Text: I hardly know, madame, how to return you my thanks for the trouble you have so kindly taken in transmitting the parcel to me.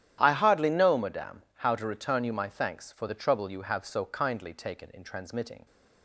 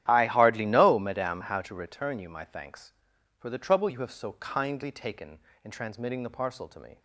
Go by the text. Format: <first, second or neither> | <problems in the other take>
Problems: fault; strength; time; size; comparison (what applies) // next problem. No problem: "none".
second | starts louder than the rest; strong; until 1.2 s; 11.5 dB; strong in the second // stops before "the parcel to me"; at 5.6 s